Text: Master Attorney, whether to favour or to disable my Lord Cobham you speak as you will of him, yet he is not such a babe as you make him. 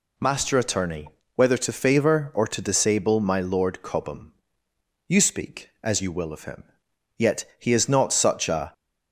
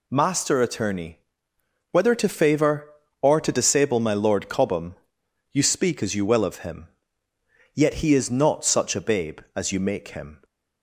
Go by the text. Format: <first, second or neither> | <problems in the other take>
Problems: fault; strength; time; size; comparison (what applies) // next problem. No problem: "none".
second | pauses between "Cobham" and "you"; noticeable; at 4.3 s; 0.76 s long; noticeable in the second // pauses between "yet" and "he"; slight; at 7.4 s; 0.16 s long // stops before "babe as you make him"; at 8.7 s